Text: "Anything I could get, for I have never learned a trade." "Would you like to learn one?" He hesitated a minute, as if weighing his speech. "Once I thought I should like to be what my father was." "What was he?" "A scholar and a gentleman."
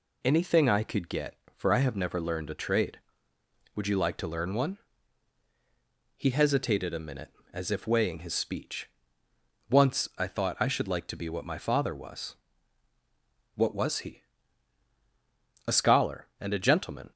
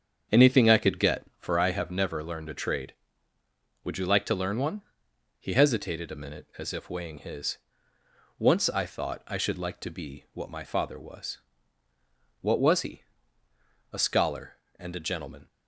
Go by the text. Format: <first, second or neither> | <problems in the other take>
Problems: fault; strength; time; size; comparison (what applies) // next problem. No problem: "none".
first | starts louder than the rest; strong; until 1.4 s; 7 dB // skips "speech"; at 7.9 s